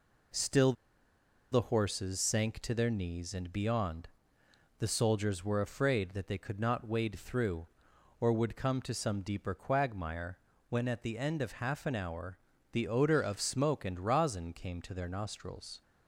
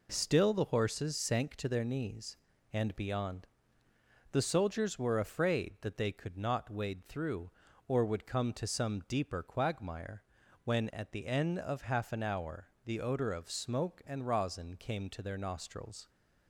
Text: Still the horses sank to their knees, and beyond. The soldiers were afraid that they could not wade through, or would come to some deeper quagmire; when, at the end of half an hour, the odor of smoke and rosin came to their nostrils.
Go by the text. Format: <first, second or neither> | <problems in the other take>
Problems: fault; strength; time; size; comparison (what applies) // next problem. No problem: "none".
second | pauses between "Still" and "the"; noticeable; at 0.7 s; 0.79 s long